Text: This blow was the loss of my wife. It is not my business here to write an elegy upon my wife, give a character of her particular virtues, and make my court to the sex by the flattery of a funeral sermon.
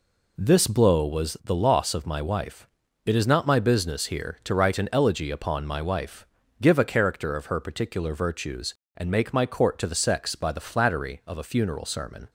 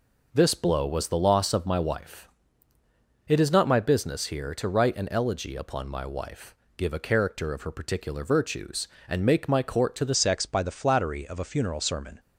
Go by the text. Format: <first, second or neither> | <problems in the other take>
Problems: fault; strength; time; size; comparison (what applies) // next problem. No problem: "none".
first | changes voice at "sex"; from 10.1 s on; 2.0 s long